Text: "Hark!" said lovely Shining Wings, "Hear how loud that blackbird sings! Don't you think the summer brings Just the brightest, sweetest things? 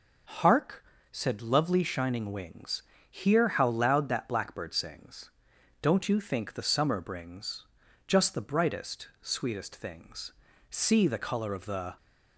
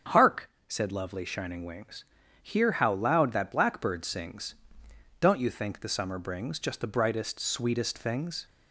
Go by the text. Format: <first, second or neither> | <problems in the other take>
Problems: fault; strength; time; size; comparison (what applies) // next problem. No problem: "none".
second | starts louder than the rest; until 1.6 s; 6.5 dB; strong in the second // pauses between "brings" and "Just"; at 7.6 s; 0.40 s long // goes on to say "See the color of the"; noticeable; from 10.7 s on; 1.2 s long